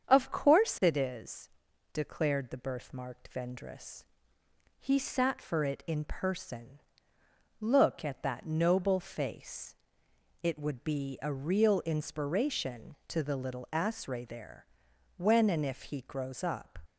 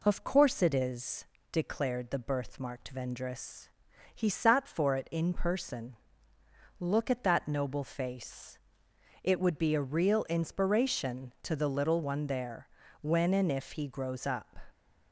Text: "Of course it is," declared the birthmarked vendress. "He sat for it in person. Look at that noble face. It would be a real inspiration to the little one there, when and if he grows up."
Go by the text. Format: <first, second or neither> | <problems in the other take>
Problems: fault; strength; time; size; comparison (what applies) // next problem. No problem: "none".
second | starts louder than the rest; strong; until 1.1 s; 7.5 dB // says "asre" for "one"; at 13.7 s